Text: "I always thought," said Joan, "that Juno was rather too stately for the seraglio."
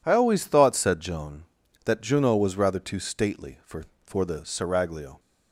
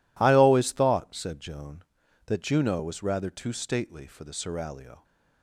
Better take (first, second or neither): second